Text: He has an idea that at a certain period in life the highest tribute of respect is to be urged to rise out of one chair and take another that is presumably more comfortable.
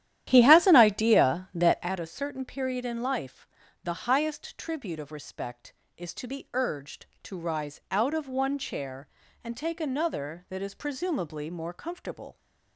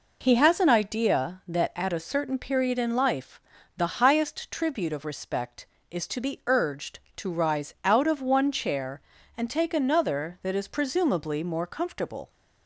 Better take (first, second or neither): second